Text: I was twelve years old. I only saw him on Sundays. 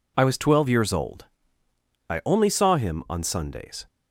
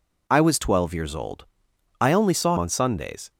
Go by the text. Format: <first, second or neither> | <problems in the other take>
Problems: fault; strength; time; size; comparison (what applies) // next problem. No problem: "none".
first | skips "him"; at 2.5 s